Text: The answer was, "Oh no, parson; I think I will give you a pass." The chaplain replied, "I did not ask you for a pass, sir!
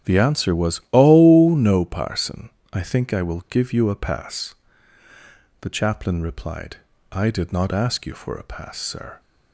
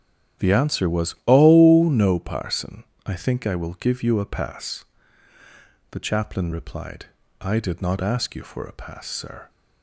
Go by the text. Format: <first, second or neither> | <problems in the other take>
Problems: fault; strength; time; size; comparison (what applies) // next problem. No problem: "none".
neither | starts louder than the rest; strong; the same in both